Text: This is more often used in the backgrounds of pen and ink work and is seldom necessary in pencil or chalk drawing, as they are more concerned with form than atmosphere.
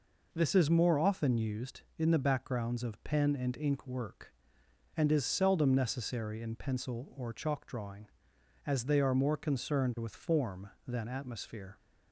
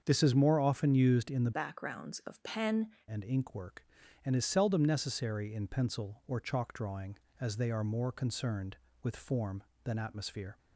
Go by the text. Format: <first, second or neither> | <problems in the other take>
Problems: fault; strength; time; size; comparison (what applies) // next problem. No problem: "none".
first | starts louder than the rest; until 1.0 s; 7 dB // changes voice from "backgrounds" to "pen"; from 1.5 to 2.9 s; 1.4 s long